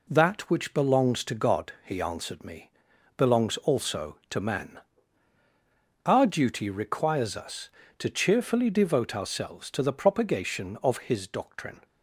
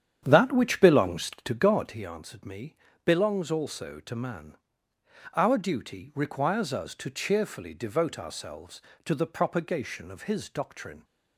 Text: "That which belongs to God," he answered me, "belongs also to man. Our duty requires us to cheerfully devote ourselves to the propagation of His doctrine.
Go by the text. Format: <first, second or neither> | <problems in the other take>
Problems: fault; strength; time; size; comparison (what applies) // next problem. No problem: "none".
first | starts louder than the rest; strong; until 2.1 s; 9 dB